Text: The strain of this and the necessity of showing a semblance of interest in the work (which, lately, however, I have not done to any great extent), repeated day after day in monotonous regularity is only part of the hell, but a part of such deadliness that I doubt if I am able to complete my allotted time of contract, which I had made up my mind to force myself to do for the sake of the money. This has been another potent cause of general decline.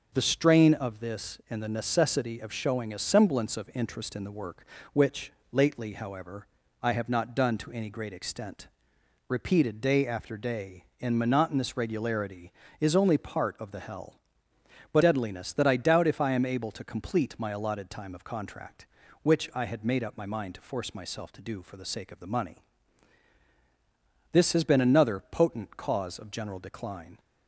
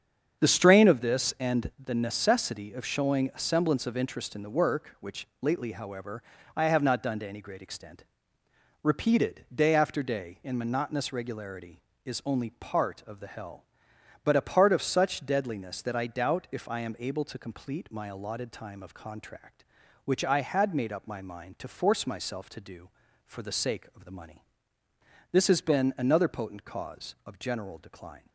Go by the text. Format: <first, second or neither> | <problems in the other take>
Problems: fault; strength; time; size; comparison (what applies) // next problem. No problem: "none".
second | starts louder than the rest; until 1.1 s; 6.5 dB; strong in the second // skips "a part of such"; at 15.0 s